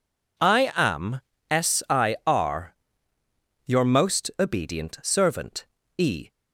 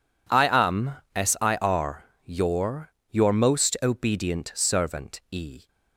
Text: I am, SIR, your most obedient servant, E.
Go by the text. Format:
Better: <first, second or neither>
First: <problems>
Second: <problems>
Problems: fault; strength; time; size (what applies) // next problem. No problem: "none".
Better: first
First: none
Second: says "your" twice; at 3.1 s